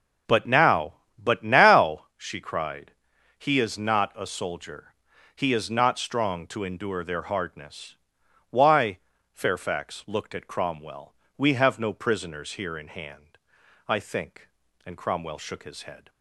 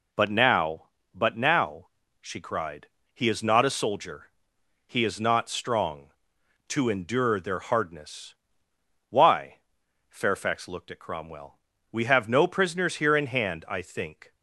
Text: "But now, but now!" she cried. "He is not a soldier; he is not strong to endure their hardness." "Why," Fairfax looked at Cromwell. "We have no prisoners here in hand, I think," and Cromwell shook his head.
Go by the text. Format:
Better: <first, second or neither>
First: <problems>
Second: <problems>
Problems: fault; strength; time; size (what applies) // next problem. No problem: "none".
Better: first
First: none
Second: stops before "and Cromwell shook his head"; at 14.3 s